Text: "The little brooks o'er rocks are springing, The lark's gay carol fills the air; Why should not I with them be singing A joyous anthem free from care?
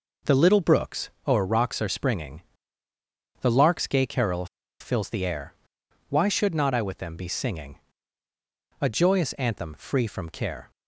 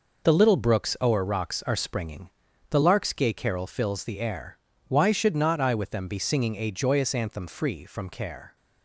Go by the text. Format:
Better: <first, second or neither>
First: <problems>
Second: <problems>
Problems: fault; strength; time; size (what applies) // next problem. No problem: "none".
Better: second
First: pauses between "brooks" and "o'er"; slight; at 1.0 s; 0.18 s long // pauses between "carol" and "fills"; slight; at 4.4 s; 0.34 s long // pauses between "singing" and "A"; at 7.7 s; 1.0 s long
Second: none